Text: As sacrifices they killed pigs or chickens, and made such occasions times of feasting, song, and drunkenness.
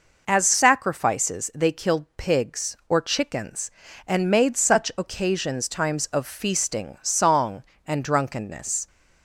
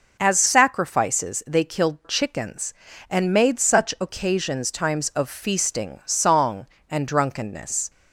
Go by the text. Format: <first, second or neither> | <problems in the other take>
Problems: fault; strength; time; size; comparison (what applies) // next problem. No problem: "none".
first | skips "pigs or"; at 2.0 s